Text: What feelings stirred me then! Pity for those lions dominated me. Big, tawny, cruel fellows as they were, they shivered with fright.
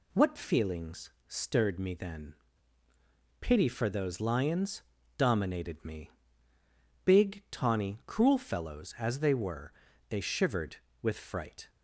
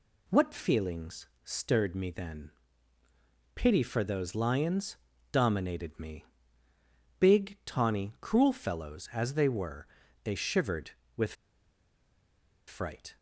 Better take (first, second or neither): first